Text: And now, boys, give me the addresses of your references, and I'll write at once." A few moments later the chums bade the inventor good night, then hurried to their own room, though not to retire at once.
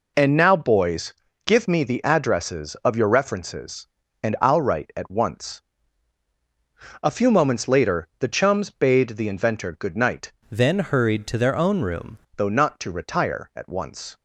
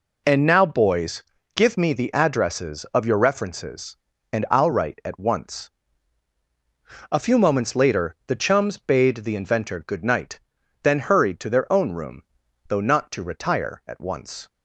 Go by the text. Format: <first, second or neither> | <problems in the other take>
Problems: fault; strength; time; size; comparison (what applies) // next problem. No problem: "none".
second | changes voice from "then" to "room"; from 10.5 to 12.1 s; 1.6 s long